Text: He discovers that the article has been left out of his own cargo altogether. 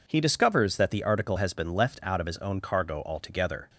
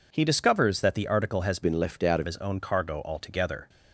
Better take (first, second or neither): first